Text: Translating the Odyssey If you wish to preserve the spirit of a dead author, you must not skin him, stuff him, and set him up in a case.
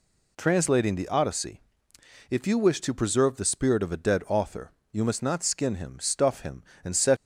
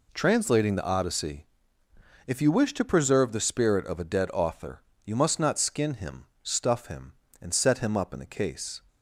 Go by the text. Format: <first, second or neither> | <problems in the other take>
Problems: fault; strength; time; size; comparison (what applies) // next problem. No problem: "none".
second | pauses between "Odyssey" and "If"; noticeable; at 1.6 s; 0.70 s long; noticeable in the second // stops before "him up in a case"; at 7.1 s